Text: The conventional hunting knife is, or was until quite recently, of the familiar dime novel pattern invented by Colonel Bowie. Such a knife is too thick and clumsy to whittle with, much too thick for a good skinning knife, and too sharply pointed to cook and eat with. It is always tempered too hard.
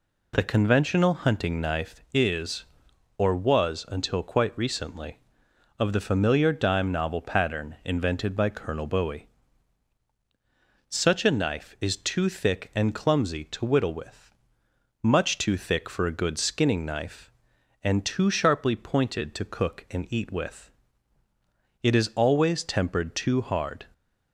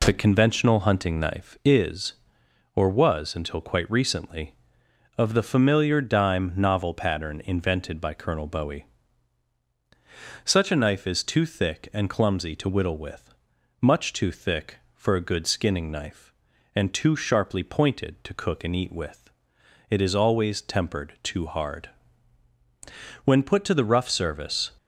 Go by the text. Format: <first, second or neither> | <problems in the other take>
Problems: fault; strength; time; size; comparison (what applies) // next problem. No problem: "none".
first | goes on to say "When put to the rough service"; from 23.2 s on; 1.4 s long